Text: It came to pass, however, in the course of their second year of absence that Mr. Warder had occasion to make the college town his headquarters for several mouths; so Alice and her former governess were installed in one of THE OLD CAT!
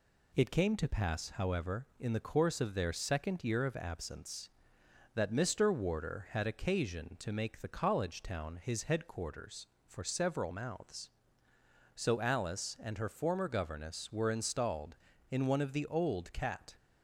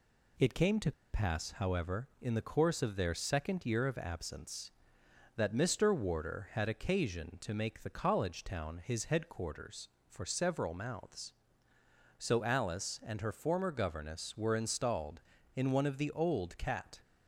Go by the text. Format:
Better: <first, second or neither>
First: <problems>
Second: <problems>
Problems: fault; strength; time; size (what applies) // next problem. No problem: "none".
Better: first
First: none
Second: pauses between "to" and "pass"; slight; at 0.9 s; 0.21 s long